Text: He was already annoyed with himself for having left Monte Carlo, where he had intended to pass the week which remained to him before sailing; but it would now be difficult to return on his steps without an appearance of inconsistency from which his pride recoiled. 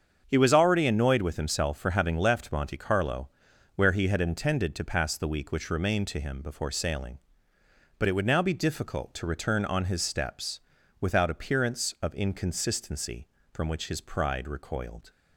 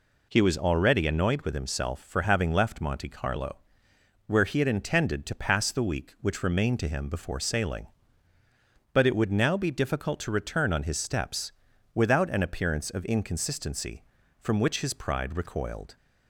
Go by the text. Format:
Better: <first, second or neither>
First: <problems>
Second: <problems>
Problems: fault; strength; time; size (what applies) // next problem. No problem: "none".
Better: second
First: starts louder than the rest; strong; until 1.2 s; 7 dB // pauses between "steps" and "without"; at 10.6 s; 0.40 s long // skips "an"; at 11.2 s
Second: pauses between "steps" and "without"; at 11.5 s; 0.42 s long